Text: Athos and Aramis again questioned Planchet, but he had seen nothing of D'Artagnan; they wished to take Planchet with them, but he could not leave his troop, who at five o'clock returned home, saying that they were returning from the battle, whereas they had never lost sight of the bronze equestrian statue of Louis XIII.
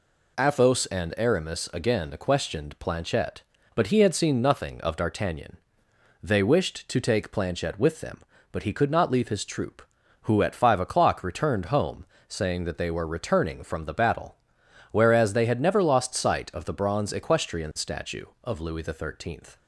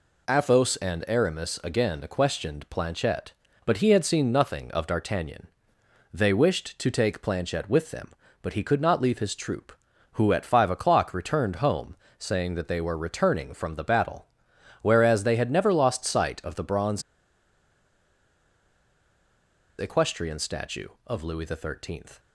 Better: first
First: none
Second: pauses between "bronze" and "equestrian"; strong; at 17.0 s; 2.7 s long

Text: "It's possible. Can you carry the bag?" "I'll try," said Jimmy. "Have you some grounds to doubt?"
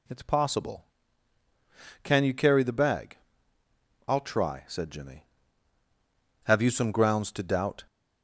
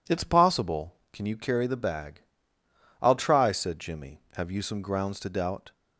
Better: neither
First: none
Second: none

